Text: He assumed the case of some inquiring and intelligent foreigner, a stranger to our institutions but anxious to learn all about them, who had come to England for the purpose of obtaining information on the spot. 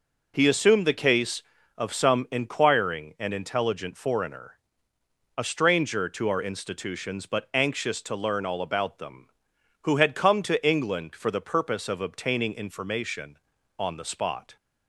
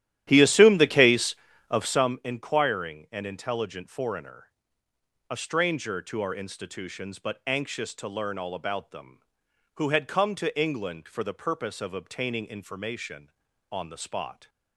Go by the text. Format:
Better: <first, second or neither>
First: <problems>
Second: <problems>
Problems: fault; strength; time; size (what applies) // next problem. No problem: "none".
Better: first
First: none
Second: starts louder than the rest; strong; until 2.1 s; 12.5 dB